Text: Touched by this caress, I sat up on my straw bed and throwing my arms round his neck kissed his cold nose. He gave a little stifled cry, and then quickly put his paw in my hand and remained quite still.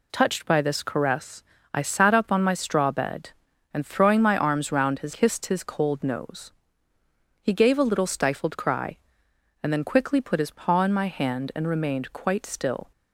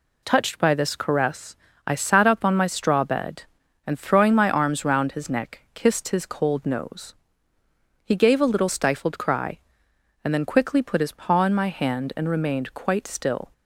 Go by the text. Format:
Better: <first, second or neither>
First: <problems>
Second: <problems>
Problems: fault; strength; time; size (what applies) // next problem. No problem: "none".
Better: second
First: skips "neck"; at 5.1 s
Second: none